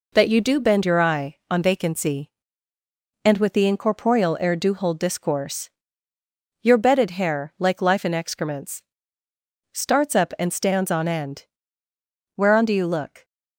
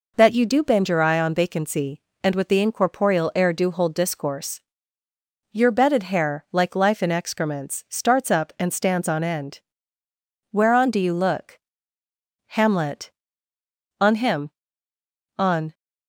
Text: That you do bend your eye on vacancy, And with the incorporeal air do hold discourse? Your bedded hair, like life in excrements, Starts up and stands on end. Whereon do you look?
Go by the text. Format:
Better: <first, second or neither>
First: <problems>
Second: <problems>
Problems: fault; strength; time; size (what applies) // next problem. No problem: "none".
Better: first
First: none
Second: goes on to say "Hamlet On him On"; strong; from 12.4 s on; 3.2 s long